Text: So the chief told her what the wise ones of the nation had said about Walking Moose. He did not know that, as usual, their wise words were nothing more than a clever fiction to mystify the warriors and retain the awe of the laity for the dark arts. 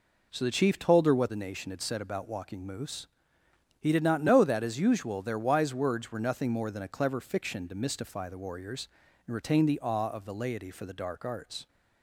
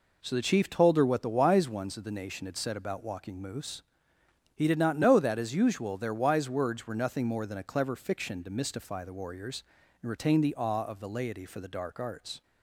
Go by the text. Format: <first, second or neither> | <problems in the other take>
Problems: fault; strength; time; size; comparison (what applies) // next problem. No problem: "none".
second | skips "the wise ones of"; at 1.3 s